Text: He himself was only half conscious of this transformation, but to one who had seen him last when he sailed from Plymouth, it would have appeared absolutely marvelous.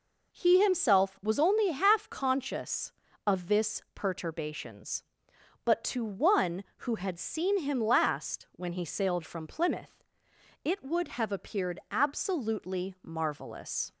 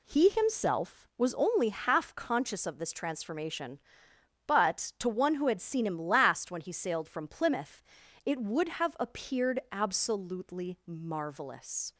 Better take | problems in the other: second | says "perturbations" for "transformation"; at 3.9 s

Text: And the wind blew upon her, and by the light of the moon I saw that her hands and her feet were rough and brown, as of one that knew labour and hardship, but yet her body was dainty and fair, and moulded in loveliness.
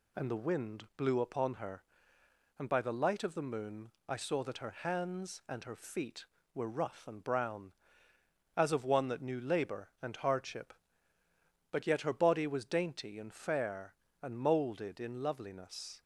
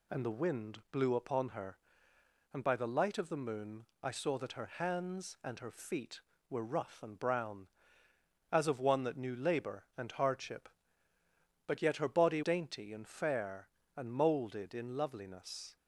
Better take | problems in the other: first | pauses between "moon" and "I"; slight; at 3.8 s; 0.18 s long; slight in the first // skips "was"; at 12.4 s

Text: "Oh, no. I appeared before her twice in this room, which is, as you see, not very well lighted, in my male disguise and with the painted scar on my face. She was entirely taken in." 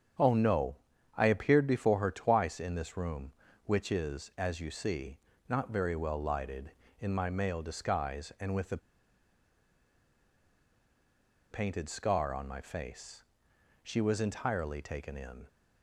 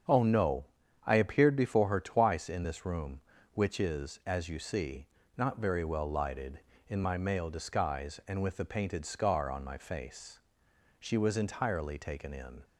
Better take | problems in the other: second | starts louder than the rest; strong; until 1.6 s; 7.5 dB; strong in the second // pauses between "the" and "painted"; strong; at 8.7 s; 2.7 s long

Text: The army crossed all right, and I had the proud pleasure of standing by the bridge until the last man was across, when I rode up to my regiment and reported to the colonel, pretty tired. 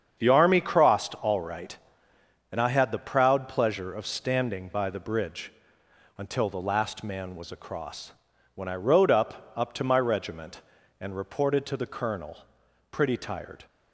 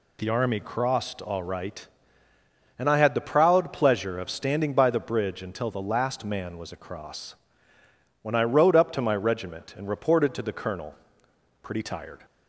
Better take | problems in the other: second | starts louder than the rest; strong; until 1.1 s; 7.5 dB // pauses between "bridge" and "until"; noticeable; at 5.5 s; 0.64 s long // says "up" twice; at 9.5 s

